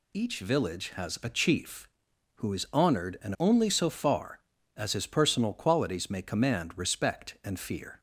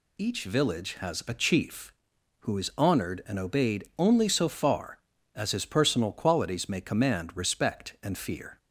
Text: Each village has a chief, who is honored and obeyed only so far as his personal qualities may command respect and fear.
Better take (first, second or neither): second